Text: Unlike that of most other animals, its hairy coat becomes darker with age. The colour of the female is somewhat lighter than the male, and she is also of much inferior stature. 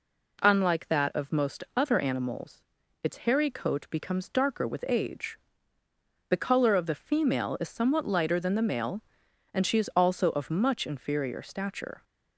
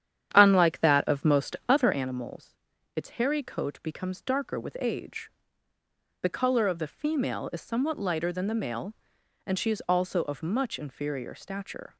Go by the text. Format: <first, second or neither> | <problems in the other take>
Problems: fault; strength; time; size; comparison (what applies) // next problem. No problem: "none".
first | starts louder than the rest; strong; until 2.0 s; 10 dB